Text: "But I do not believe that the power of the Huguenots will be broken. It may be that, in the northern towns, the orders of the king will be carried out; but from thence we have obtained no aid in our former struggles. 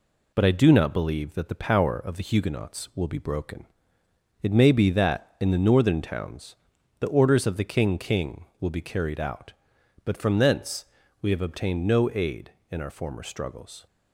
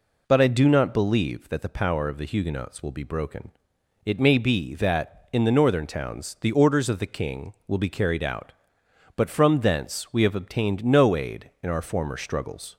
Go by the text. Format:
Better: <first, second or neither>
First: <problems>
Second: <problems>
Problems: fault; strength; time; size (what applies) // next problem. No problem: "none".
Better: second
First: says "king" twice; at 7.9 s // pauses between "thence" and "we"; slight; at 10.8 s; 0.34 s long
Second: none